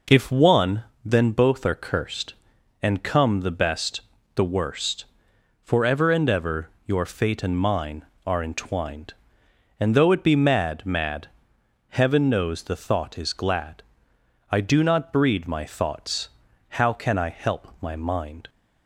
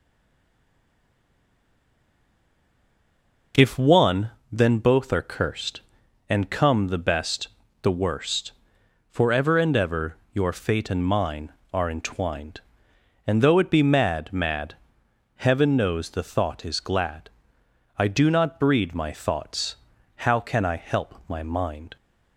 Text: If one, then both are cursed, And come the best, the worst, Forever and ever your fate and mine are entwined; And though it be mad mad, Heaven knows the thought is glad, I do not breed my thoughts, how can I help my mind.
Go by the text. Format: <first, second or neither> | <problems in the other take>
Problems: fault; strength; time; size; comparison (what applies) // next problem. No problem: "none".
first | stays silent before the first word; strong; until 3.5 s; 3.5 s long // pauses between "ever" and "your"; slight; at 10.1 s; 0.18 s long; slight in the first